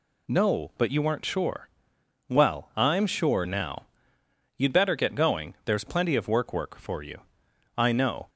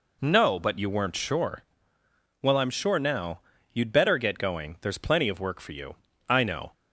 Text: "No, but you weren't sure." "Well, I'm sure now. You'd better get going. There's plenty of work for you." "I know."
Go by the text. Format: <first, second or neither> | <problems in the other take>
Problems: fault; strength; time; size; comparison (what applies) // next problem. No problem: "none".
second | says "work" twice; at 6.5 s